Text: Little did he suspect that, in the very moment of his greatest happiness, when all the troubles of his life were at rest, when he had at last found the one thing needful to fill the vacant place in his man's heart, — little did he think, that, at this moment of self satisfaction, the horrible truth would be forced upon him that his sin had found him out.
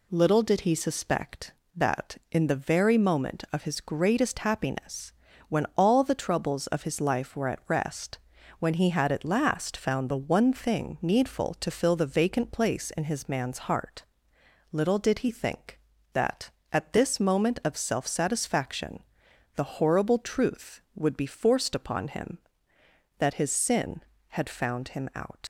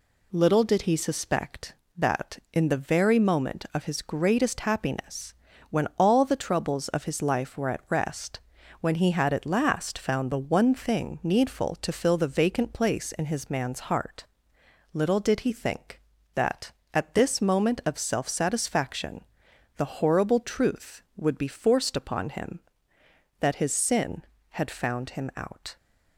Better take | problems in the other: second | leaves "out" unfinished; at 25.4 s; 75 ms

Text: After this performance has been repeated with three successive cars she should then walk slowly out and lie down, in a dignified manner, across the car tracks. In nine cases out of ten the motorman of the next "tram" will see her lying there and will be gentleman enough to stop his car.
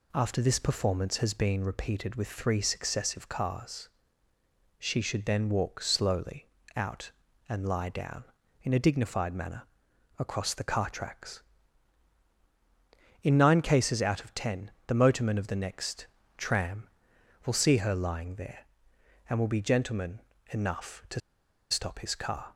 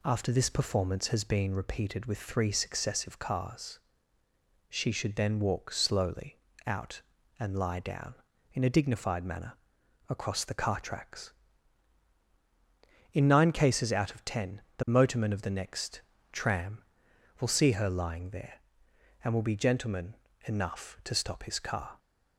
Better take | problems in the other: second | pauses between "cars" and "she"; noticeable; at 3.8 s; 0.90 s long; noticeable in the second // pauses between "slowly" and "out"; slight; at 6.4 s; 0.28 s long; slight in the second // pauses between "ten" and "the"; slight; at 14.7 s; 0.16 s long; slight in the second // pauses between "next" and "tram"; slight; at 16.0 s; 0.28 s long; slight in the second // pauses between "gentleman" and "enough"; slight; at 20.1 s; 0.30 s long; slight in the second // pauses between "to" and "stop"; noticeable; at 21.2 s; 0.51 s long

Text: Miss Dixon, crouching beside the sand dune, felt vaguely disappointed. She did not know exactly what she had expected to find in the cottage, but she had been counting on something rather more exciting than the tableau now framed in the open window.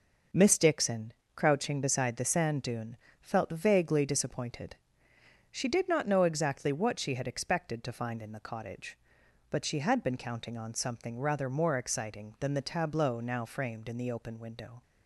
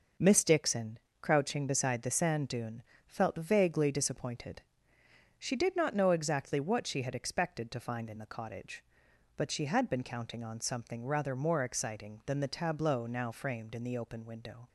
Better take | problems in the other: neither | none

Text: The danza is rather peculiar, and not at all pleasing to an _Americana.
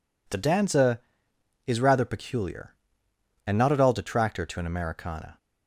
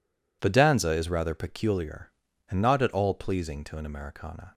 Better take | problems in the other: second | says "detractor" for "pleasing"; at 3.9 s

